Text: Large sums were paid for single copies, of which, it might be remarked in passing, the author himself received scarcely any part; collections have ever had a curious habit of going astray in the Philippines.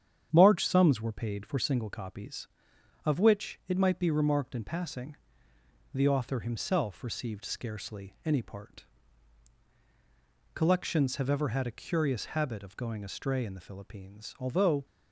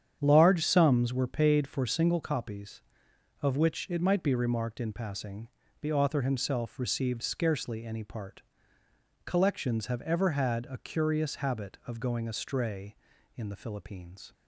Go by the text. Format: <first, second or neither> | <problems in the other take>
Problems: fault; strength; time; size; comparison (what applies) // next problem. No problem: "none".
second | starts louder than the rest; strong; until 1.3 s; 9 dB; strong in the second // goes on to say "Although"; slight; from 14.3 s on; 0.46 s long